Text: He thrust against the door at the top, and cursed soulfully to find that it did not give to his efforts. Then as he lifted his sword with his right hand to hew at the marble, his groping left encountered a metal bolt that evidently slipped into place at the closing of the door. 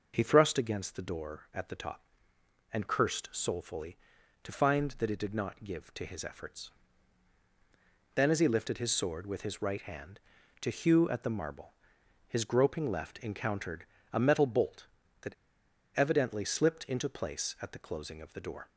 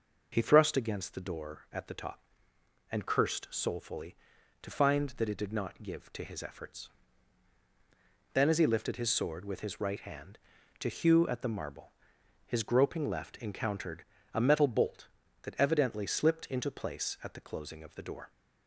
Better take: second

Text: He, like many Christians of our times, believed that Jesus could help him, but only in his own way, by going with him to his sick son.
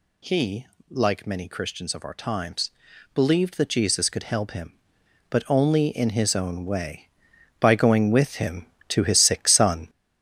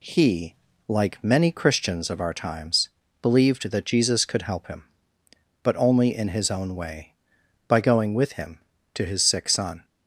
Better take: second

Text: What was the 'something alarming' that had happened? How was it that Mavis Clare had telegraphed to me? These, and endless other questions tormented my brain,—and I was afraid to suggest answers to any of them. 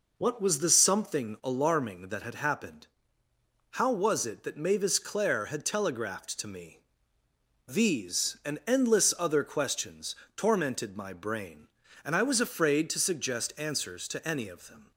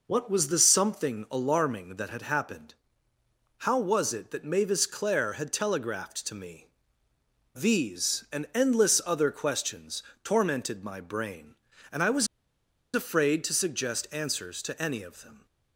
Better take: first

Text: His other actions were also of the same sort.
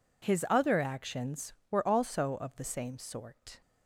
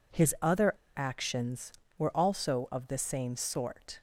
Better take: first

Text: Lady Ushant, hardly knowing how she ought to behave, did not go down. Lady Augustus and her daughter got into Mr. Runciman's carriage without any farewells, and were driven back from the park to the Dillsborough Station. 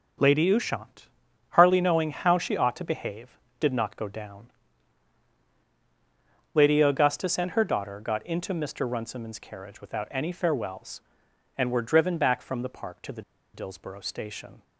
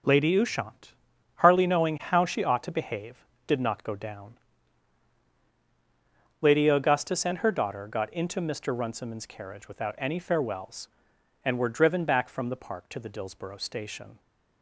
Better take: second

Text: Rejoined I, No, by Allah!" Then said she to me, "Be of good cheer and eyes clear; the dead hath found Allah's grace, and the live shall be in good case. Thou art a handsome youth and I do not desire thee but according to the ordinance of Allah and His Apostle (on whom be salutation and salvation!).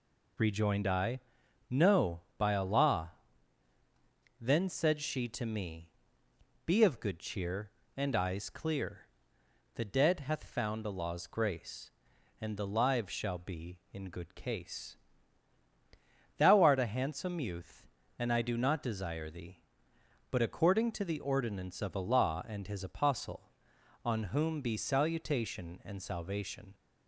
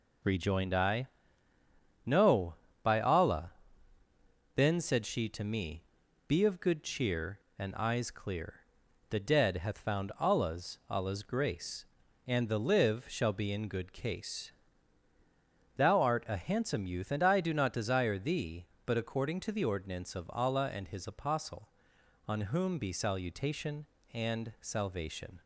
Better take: first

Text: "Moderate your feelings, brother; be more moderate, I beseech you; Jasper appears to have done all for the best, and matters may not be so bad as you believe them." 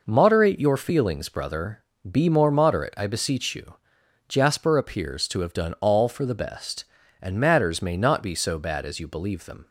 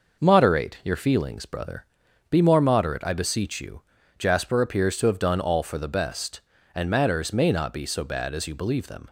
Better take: neither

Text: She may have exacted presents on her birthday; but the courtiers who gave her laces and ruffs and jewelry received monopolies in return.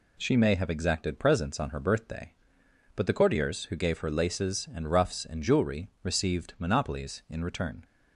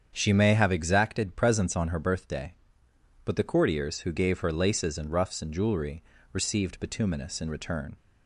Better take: first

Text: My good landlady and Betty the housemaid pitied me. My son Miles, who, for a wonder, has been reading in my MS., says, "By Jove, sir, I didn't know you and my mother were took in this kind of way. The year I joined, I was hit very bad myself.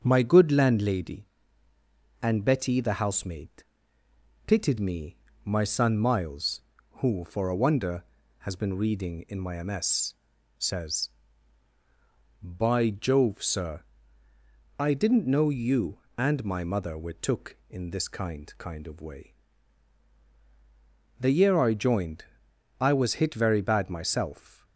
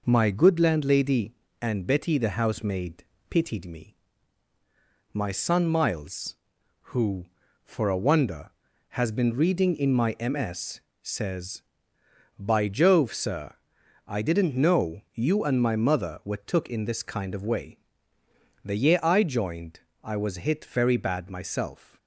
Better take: second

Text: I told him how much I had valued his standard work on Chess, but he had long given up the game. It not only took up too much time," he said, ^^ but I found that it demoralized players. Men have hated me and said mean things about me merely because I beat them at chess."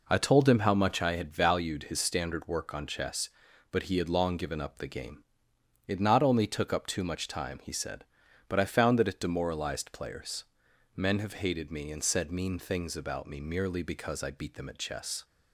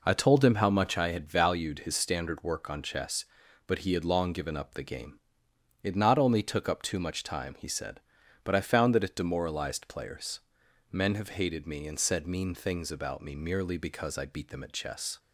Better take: neither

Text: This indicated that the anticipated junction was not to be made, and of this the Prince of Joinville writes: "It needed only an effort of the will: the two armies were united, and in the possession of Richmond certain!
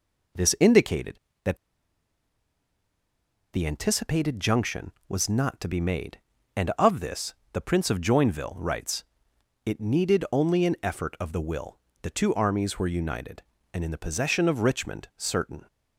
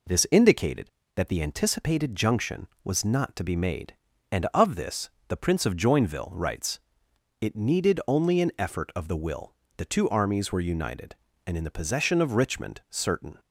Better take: second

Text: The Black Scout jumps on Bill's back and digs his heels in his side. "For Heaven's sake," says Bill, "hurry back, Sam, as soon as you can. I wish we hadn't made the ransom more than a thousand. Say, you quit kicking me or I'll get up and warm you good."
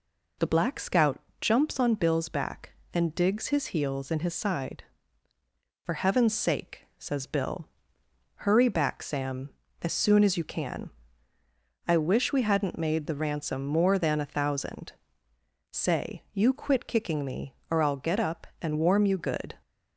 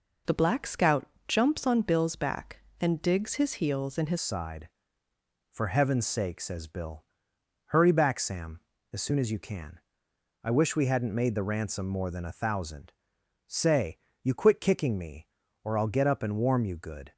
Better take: first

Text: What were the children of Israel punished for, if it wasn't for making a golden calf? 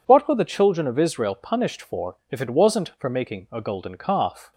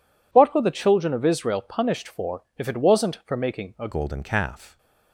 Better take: first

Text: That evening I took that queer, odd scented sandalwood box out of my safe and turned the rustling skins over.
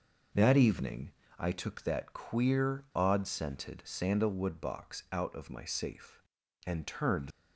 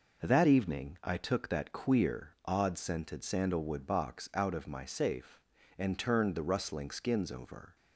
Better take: second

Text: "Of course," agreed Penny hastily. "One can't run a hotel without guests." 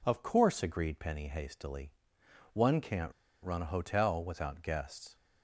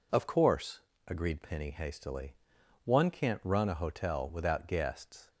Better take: second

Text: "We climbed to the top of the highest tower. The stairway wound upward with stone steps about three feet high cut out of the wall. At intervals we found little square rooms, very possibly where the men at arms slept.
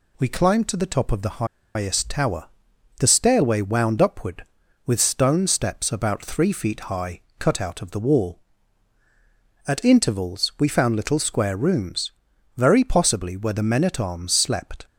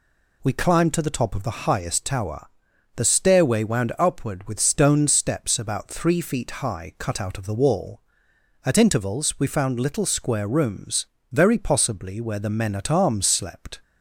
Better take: second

